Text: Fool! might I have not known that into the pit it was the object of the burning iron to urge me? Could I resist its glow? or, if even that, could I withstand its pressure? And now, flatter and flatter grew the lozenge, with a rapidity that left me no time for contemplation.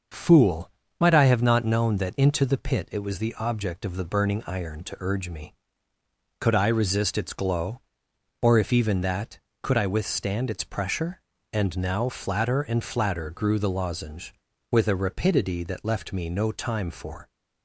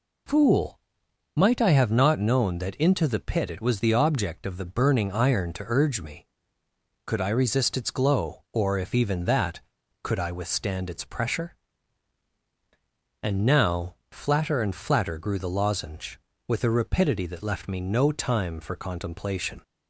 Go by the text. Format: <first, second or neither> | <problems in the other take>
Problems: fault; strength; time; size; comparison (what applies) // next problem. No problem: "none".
second | starts louder than the rest; noticeable; until 1.4 s; 6 dB // stops before "contemplation"; at 17.2 s